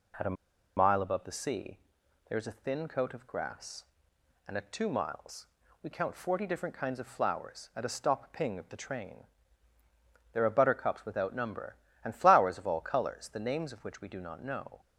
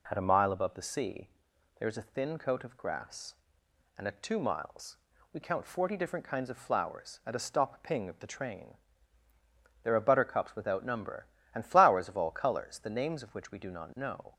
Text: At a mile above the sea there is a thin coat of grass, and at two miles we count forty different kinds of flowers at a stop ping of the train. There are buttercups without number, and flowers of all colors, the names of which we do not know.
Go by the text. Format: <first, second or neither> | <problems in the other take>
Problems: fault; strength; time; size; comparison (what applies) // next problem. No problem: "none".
second | pauses between "a" and "mile"; at 0.3 s; 0.42 s long // pauses between "sea" and "there"; noticeable; at 1.7 s; 0.54 s long; noticeable in the second // pauses between "miles" and "we"; slight; at 5.4 s; 0.36 s long; slight in the second